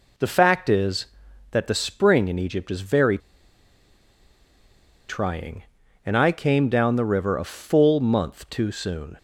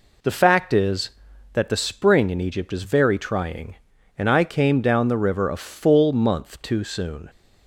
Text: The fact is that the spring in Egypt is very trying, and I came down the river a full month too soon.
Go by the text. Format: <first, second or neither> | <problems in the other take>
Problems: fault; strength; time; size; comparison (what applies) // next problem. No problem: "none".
second | pauses between "very" and "trying"; strong; at 3.1 s; 1.9 s long